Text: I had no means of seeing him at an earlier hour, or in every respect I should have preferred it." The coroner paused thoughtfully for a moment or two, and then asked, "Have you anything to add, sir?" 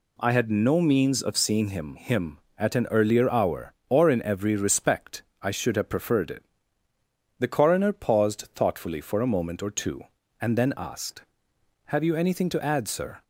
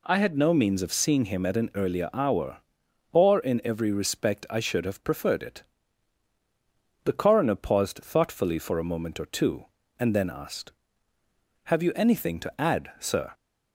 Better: second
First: says "him" twice; at 1.9 s // pauses between "respect" and "I"; slight; at 5.2 s; 0.20 s long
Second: none

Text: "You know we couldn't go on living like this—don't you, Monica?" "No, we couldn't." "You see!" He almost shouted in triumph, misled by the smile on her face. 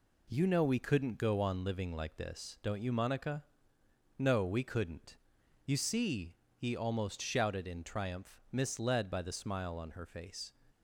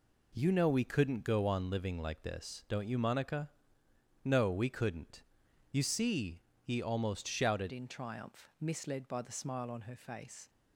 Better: first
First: none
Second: changes voice at "in"; from 7.7 s on; 2.7 s long

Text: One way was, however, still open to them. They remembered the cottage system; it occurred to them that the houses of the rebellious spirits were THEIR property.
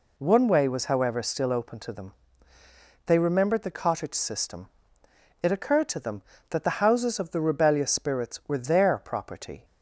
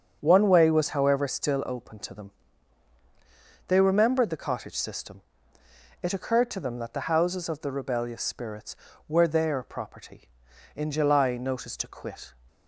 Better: first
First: none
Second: starts louder than the rest; until 1.2 s; 6.5 dB // goes on to say "In July notice to quit"; from 10.7 s on; 1.6 s long

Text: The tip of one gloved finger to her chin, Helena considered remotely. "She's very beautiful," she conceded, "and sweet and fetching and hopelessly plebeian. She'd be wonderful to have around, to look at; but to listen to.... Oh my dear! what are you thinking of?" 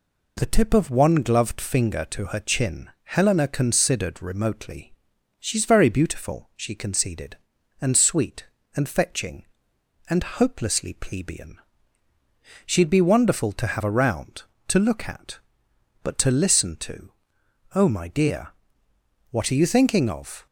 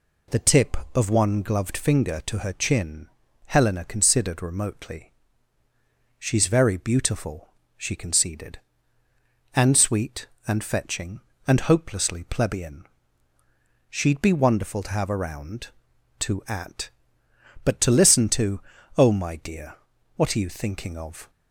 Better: first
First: none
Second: skips "look"; at 16.4 s

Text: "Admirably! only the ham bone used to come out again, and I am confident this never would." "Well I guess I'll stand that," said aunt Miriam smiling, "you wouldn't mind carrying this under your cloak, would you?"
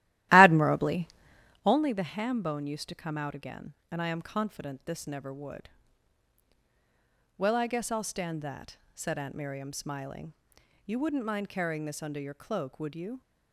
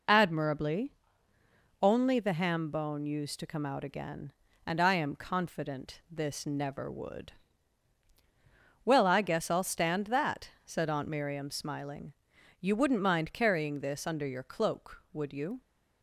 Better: second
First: starts louder than the rest; strong; until 1.7 s; 15 dB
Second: none

